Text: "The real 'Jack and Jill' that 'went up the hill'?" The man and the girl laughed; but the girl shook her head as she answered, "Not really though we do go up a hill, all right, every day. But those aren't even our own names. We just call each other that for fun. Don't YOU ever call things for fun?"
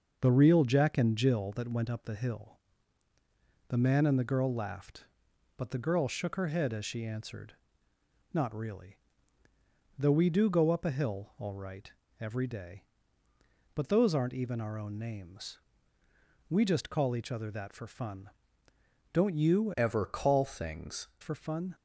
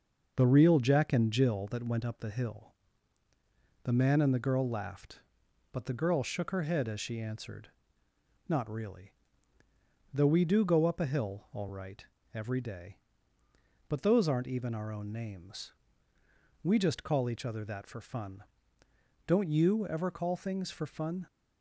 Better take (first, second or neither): second